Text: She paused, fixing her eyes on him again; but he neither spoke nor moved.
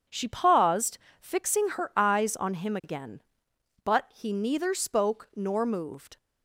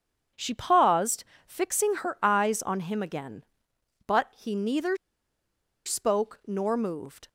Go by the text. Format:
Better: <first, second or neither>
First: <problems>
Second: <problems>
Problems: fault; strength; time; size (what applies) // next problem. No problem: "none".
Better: first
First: starts louder than the rest; strong; until 1.3 s; 8 dB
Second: starts louder than the rest; strong; until 1.5 s; 8 dB // pauses between "neither" and "spoke"; noticeable; at 4.9 s; 0.88 s long